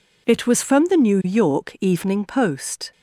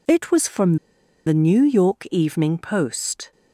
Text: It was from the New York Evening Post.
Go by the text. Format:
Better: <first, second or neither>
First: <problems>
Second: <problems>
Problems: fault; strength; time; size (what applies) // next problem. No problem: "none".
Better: first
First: none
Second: pauses between "from" and "the"; noticeable; at 0.7 s; 0.51 s long